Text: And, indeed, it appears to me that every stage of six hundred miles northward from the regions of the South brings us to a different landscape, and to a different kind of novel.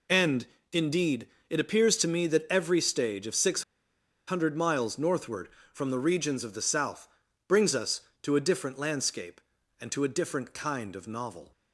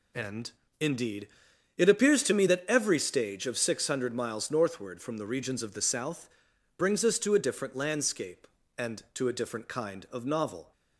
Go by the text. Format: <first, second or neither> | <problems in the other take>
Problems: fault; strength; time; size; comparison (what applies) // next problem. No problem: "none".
second | pauses between "six" and "hundred"; noticeable; at 3.6 s; 0.65 s long // pauses between "South" and "brings"; at 7.0 s; 0.40 s long; noticeable in the second